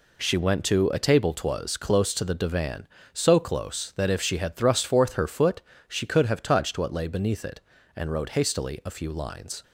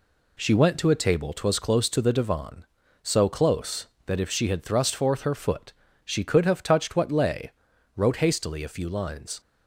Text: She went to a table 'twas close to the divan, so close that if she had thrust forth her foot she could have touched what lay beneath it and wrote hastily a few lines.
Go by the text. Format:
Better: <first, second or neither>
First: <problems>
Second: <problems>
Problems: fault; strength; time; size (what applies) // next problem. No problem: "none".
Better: first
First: pauses between "foot" and "she"; slight; at 5.6 s; 0.26 s long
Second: pauses between "foot" and "she"; slight; at 5.7 s; 0.32 s long // skips "beneath it and"; at 7.7 s